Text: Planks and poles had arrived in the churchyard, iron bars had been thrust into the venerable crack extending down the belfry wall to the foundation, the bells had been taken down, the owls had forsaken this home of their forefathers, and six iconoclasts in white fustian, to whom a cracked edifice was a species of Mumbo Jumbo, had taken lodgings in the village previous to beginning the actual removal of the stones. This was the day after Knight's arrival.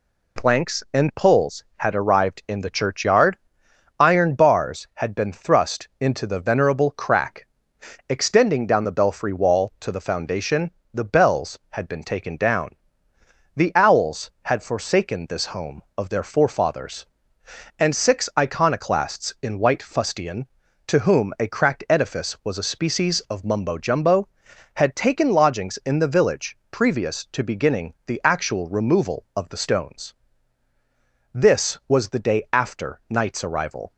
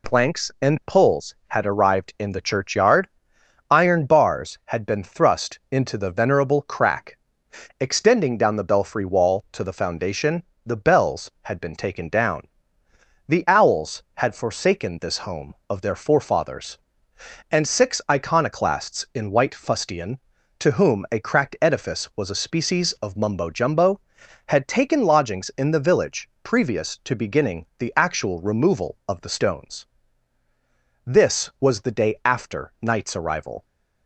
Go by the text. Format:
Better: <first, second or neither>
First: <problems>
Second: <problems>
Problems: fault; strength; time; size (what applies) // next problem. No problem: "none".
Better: neither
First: pauses between "crack" and "extending"; noticeable; at 7.4 s; 0.60 s long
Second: pauses between "crack" and "extending"; noticeable; at 7.1 s; 0.60 s long